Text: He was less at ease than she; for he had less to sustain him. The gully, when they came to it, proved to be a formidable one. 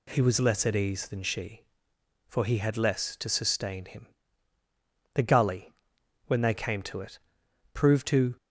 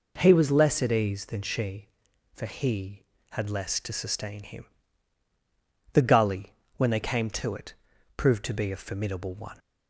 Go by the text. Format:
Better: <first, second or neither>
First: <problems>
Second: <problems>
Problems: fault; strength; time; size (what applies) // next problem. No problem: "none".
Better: second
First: stops before "be a formidable one"; at 8.3 s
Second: none